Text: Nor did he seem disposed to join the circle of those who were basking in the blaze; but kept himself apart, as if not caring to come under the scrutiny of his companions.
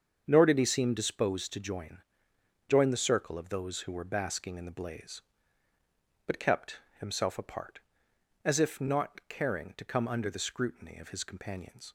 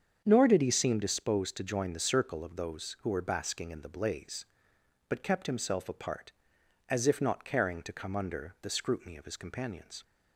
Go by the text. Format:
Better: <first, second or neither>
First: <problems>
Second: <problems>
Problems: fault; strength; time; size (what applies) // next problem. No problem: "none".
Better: second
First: starts louder than the rest; until 1.2 s; 7 dB // says "join" twice; at 2.6 s // pauses between "kept" and "himself"; slight; at 6.7 s; 0.20 s long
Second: starts louder than the rest; strong; until 1.2 s; 7.5 dB